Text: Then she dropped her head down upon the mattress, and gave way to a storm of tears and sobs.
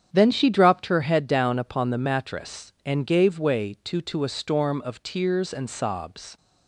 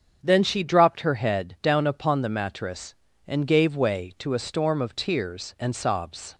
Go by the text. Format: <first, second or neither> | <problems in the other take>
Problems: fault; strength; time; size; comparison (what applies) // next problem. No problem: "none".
second | starts louder than the rest; strong; until 1.1 s; 9 dB; strong in the second // says "to" twice; at 4.0 s